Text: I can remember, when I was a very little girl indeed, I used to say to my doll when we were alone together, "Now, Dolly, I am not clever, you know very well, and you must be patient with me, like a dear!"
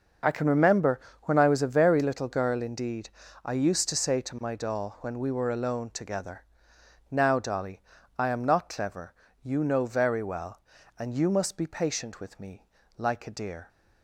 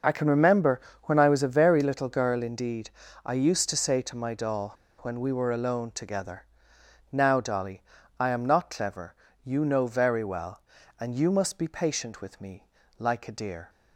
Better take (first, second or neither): first